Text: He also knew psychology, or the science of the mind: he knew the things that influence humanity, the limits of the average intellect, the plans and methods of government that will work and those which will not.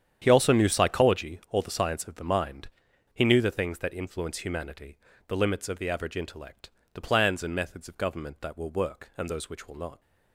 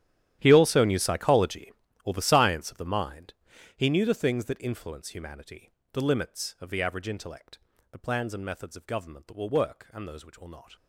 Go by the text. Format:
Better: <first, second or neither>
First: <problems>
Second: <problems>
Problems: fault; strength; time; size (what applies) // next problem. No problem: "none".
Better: first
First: starts louder than the rest; strong; until 1.2 s; 9 dB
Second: gets quieter; strong; throughout; 19 dB // starts louder than the rest; strong; until 1.4 s; 11.5 dB